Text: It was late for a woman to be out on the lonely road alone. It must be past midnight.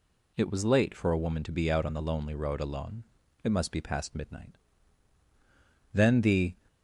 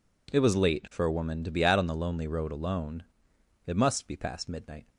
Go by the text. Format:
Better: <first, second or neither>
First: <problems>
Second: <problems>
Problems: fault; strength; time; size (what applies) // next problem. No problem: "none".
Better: second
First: goes on to say "Then the"; noticeable; from 5.9 s on; 0.62 s long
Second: none